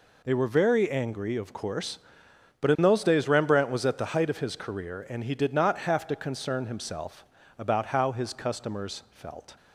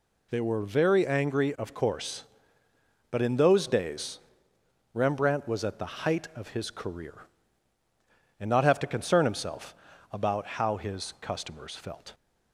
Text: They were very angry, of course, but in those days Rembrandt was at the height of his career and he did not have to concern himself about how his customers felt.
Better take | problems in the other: first | pauses between "days" and "Rembrandt"; noticeable; at 4.1 s; 0.76 s long // skips "he did"; at 8.4 s // pauses between "himself" and "about"; at 9.7 s; 0.38 s long; slight in the first

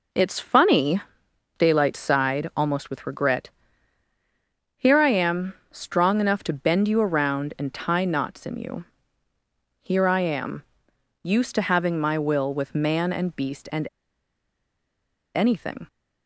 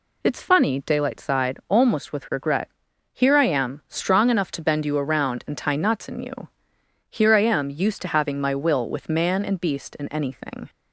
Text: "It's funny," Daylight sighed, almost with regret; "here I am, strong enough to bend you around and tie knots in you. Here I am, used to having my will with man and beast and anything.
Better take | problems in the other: second | pauses between "and" and "anything"; strong; at 13.8 s; 1.4 s long

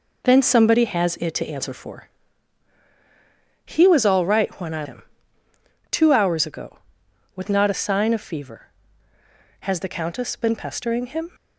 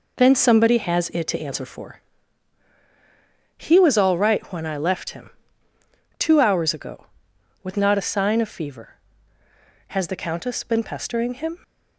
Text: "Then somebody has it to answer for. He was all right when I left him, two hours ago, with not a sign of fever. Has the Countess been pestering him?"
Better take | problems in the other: second | skips "left"; at 4.8 s

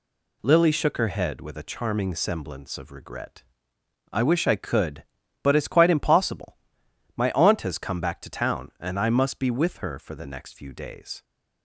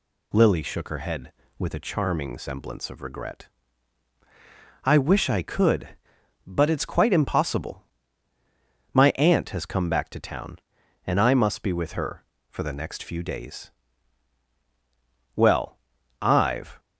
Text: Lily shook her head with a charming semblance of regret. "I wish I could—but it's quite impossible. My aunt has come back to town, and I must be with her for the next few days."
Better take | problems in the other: first | goes on to say "Well I've"; from 15.3 s on; 1.4 s long

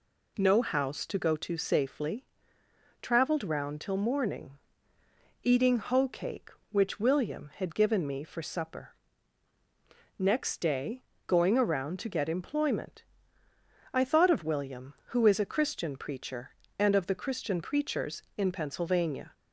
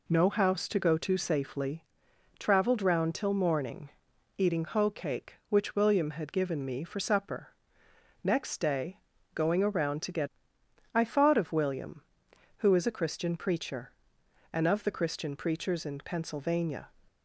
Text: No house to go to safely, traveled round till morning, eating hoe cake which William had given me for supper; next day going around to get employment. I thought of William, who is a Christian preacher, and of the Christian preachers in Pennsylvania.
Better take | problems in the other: first | pauses between "day" and "going"; slight; at 8.9 s; 0.36 s long; slight in the first // skips "employment"; at 10.5 s

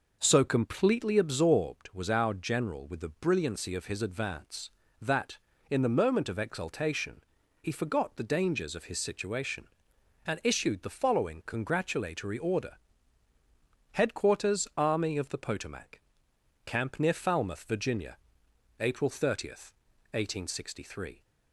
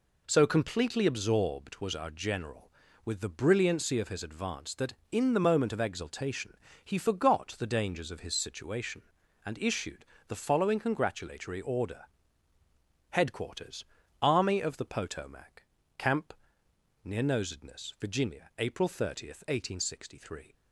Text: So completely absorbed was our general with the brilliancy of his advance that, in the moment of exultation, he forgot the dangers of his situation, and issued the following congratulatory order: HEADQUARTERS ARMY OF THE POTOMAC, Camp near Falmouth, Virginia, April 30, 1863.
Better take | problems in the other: first | pauses between "issued" and "the"; slight; at 10.0 s; 0.24 s long // pauses between "HEADQUARTERS" and "ARMY"; at 13.8 s; 0.38 s long // pauses between "Camp" and "near"; noticeable; at 16.3 s; 0.70 s long // says "Nosedness" for "Falmouth"; at 17.2 s

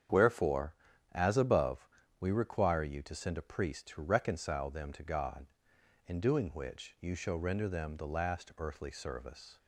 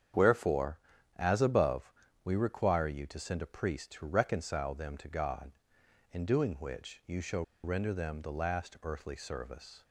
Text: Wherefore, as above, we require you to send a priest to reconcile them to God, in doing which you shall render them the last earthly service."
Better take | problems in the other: first | starts louder than the rest; strong; until 1.5 s; 8 dB; strong in the first // pauses between "shall" and "render"; slight; at 7.4 s; 0.20 s long

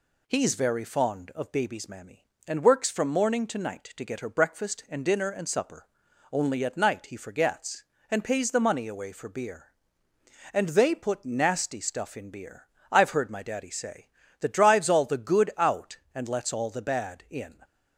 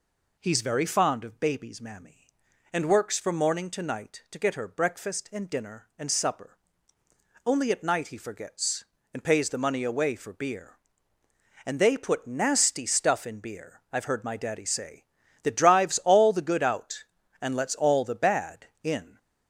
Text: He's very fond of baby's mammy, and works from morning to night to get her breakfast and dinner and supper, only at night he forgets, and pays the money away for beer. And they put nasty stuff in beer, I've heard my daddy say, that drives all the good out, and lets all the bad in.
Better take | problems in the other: neither | none

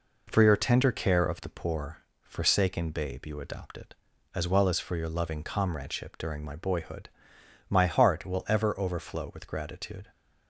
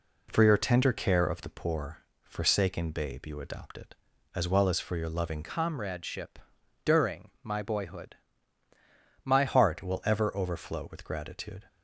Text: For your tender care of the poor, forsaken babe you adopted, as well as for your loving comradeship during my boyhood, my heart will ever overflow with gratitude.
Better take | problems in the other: first | changes voice from "comradeship" to "my"; from 5.4 to 9.4 s; 4.0 s long // pauses between "comradeship" and "during"; noticeable; at 6.3 s; 0.48 s long

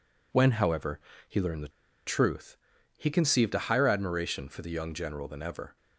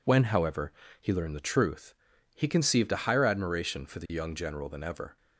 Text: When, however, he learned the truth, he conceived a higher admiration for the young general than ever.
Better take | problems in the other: second | pauses between "the" and "truth"; at 1.6 s; 0.38 s long

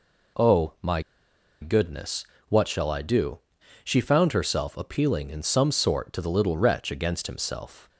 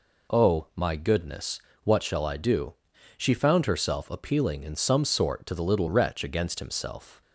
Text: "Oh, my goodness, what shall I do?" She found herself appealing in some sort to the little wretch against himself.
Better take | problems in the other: second | pauses between "my" and "goodness"; noticeable; at 1.0 s; 0.59 s long

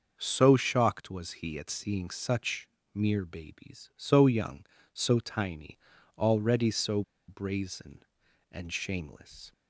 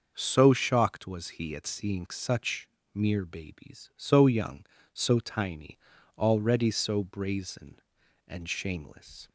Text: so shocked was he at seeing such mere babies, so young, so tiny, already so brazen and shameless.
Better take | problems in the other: second | starts louder than the rest; noticeable; until 1.1 s; 6 dB; noticeable in the second // pauses between "such" and "mere"; slight; at 2.6 s; 0.26 s long; slight in the second // pauses between "so" and "brazen"; slight; at 7.0 s; 0.25 s long

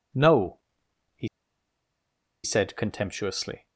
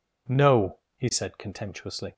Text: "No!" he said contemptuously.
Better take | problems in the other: second | pauses between "he" and "said"; at 1.2 s; 1.1 s long

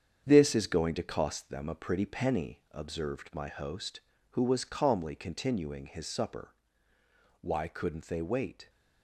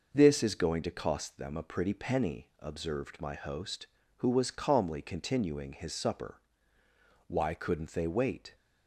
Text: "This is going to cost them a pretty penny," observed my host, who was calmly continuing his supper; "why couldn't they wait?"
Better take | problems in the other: second | gets quieter; throughout; 7 dB

